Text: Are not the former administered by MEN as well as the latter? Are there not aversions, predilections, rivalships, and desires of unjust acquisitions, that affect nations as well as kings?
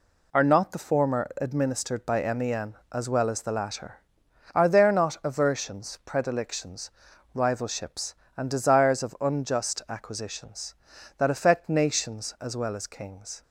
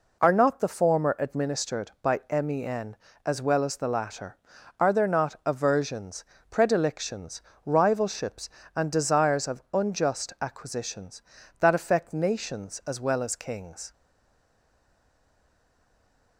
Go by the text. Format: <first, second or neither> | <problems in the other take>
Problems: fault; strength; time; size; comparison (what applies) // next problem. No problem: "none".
first | stays silent after the last word; from 13.9 s on; 2.4 s long